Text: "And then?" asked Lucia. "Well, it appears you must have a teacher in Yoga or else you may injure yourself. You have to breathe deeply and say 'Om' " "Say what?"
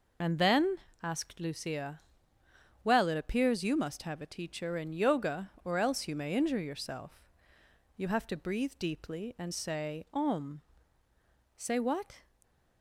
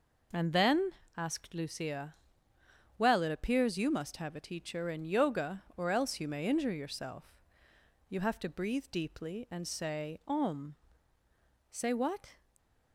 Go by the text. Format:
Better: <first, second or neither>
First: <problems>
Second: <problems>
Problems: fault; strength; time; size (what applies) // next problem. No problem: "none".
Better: second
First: loses the start of "And"; at 0.2 s; 40 ms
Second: none